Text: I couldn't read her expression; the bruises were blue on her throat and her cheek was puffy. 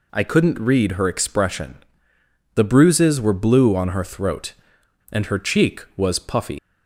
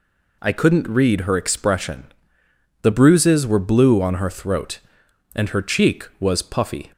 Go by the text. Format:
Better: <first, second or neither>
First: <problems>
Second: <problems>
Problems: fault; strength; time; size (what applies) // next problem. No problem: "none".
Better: second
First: leaves "puffy" unfinished; at 6.5 s; 95 ms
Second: none